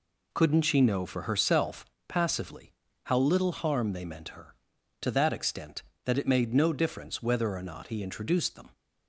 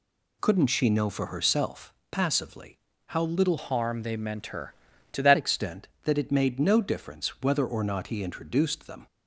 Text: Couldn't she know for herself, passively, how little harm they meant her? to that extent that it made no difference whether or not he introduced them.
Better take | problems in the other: first | changes voice from "harm" to "that"; from 3.5 to 5.3 s; 1.8 s long

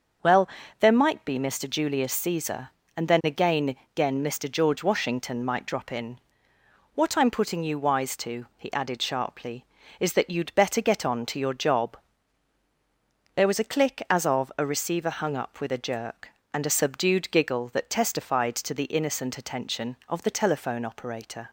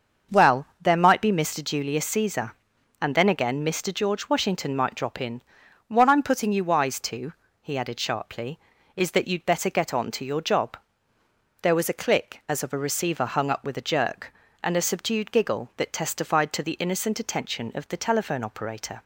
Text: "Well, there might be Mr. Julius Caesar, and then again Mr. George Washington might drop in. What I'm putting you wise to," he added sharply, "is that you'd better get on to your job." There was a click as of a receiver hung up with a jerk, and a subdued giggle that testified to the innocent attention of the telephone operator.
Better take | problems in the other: second | starts louder than the rest; until 1.5 s; 6 dB; also in the second // says "again" twice; at 3.9 s

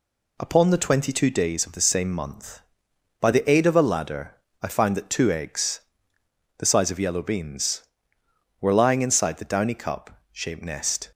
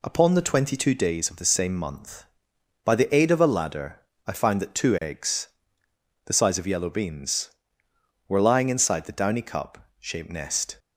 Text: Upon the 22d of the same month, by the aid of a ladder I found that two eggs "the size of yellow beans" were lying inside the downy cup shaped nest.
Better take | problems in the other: neither | pauses between "ladder" and "I"; slight; the same in both // pauses between "eggs" and "the"; noticeable; the same in both

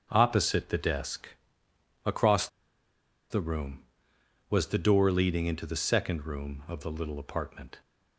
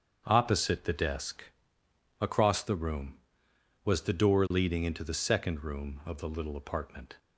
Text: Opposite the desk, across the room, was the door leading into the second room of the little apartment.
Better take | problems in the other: second | starts louder than the rest; strong; until 1.1 s; 8 dB; strong in the second // pauses between "across" and "the"; noticeable; at 2.4 s; 0.83 s long

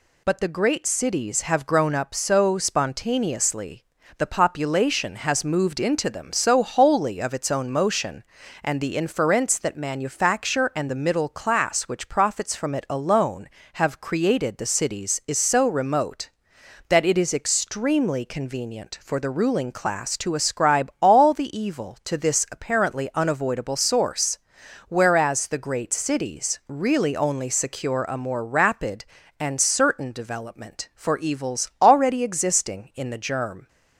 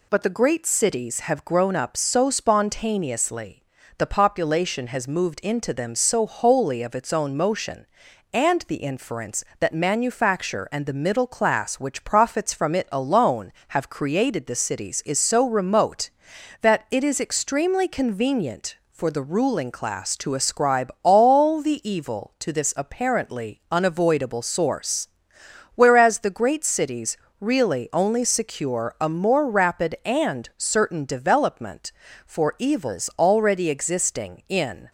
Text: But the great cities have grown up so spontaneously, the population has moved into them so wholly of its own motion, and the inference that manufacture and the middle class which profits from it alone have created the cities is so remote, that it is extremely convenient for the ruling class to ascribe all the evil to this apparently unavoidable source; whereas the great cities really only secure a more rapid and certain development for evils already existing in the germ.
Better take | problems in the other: first | pauses between "cities" and "really"; slight; at 27.1 s; 0.24 s long // stops before "the germ"; at 34.8 s

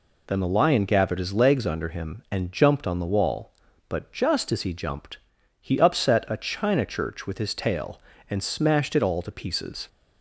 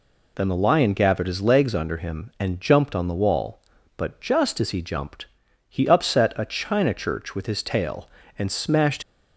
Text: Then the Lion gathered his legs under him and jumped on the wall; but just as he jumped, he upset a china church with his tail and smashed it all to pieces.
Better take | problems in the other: first | stops before "it all to pieces"; at 9.0 s

